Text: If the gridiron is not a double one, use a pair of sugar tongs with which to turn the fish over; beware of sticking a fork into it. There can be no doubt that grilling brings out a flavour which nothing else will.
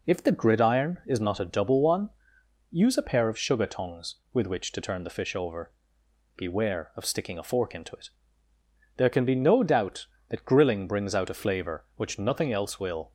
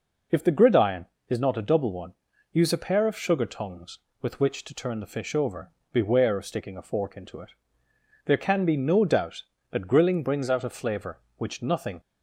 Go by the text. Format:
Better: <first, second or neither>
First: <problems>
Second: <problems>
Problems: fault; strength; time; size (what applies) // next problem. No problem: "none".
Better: first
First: none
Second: stops before "else will"; at 11.9 s